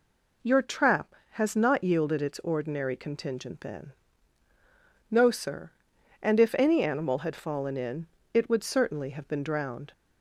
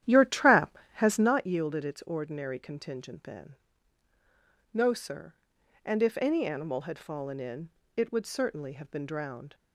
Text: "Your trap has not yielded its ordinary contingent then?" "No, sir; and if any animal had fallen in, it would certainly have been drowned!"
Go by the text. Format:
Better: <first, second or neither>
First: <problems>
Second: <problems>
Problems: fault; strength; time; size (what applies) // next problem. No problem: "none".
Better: first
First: none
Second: starts louder than the rest; strong; until 1.4 s; 11 dB